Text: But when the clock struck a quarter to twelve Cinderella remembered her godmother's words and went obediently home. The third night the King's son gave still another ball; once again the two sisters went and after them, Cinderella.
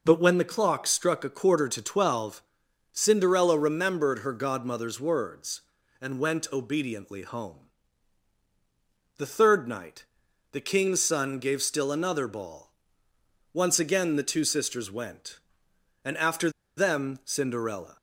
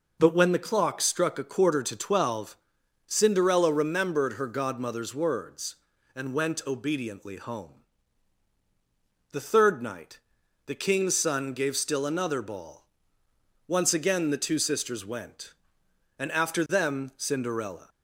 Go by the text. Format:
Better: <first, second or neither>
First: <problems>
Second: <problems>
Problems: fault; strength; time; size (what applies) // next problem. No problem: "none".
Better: second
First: pauses between "twelve" and "Cinderella"; noticeable; at 2.4 s; 0.54 s long // pauses between "night" and "the"; noticeable; at 10.0 s; 0.48 s long // pauses between "after" and "them"; slight; at 16.4 s; 0.27 s long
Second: pauses between "twelve" and "Cinderella"; noticeable; at 2.5 s; 0.54 s long // pauses between "night" and "the"; noticeable; at 10.1 s; 0.48 s long